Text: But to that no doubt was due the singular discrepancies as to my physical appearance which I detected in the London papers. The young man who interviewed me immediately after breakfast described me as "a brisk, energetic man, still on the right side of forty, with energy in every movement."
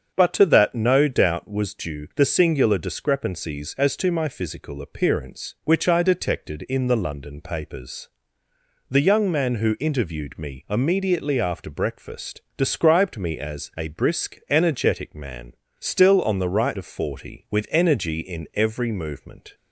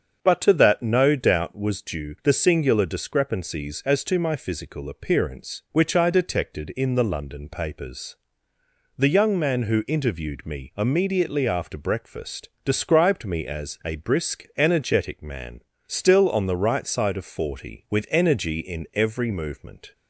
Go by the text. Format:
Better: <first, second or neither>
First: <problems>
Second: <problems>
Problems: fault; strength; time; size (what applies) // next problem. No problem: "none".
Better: second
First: starts louder than the rest; until 1.1 s; 7 dB // pauses between "breakfast" and "described"; slight; at 12.4 s; 0.16 s long // skips "side"; at 16.7 s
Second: starts louder than the rest; until 1.2 s; 7 dB // pauses between "breakfast" and "described"; slight; at 12.5 s; 0.16 s long